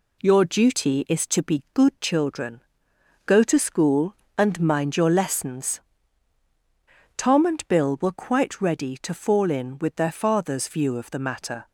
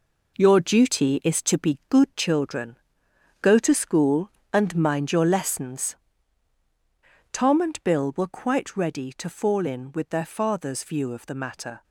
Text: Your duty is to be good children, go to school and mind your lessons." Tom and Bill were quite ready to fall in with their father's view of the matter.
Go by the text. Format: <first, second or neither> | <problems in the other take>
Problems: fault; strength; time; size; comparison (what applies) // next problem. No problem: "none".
first | gets quieter; strong; throughout; 10 dB